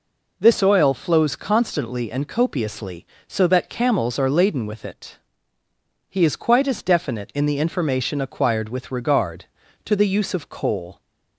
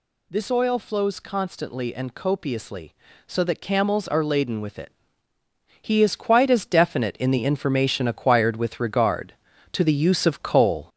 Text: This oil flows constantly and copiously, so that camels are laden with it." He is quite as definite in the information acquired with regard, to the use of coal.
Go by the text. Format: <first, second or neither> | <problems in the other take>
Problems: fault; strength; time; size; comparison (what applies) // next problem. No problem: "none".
first | gets louder; noticeable; throughout; 5 dB